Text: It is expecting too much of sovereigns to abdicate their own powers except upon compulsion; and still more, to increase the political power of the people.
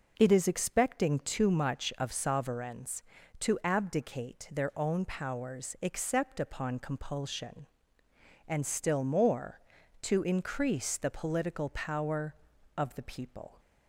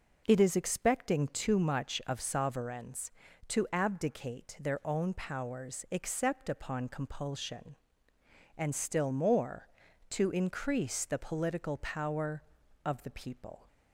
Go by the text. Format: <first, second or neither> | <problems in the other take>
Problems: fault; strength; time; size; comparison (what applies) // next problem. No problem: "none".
neither | none